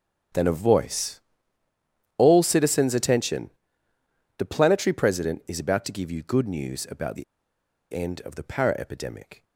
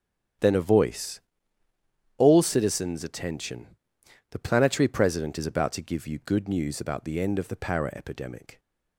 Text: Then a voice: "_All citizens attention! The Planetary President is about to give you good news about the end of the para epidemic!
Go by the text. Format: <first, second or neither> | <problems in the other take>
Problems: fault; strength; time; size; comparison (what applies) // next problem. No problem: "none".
second | starts louder than the rest; strong; until 2.3 s; 8.5 dB; strong in the second // pauses between "the" and "end"; noticeable; at 7.2 s; 0.69 s long